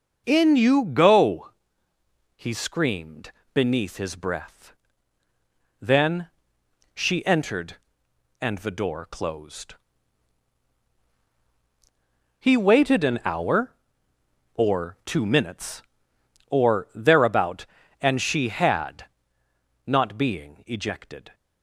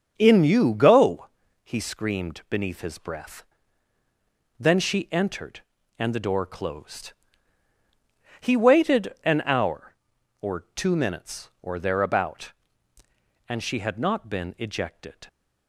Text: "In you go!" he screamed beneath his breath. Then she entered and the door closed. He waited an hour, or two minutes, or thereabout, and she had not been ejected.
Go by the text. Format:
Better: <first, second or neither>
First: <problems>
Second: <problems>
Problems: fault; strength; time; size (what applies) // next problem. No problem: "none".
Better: second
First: starts louder than the rest; until 1.2 s; 6 dB // pauses between "screamed" and "beneath"; slight; at 3.3 s; 0.22 s long // pauses between "Then" and "she"; noticeable; at 6.3 s; 0.64 s long // pauses between "had" and "not"; noticeable; at 19.0 s; 0.80 s long // says "being" for "been"; at 20.1 s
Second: starts louder than the rest; until 1.1 s; 6.5 dB